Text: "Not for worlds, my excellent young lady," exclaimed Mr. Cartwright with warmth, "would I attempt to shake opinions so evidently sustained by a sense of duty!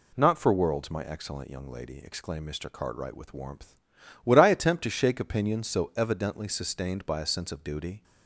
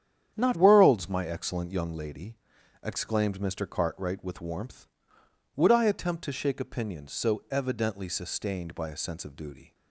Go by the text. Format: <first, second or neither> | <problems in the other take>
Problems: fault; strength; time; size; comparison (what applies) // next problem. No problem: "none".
first | starts louder than the rest; strong; until 1.3 s; 9 dB // skips "for"; at 0.5 s